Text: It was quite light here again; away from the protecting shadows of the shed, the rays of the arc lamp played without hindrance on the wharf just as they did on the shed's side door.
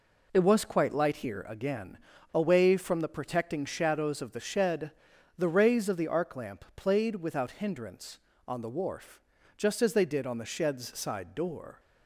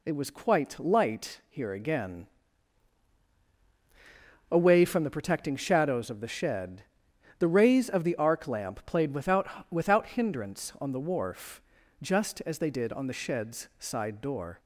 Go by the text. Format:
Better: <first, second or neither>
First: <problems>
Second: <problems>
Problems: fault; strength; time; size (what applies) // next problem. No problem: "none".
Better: first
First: pauses between "wharf" and "just"; slight; at 9.1 s; 0.36 s long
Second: says "without" twice; at 9.7 s // pauses between "wharf" and "just"; at 11.6 s; 0.40 s long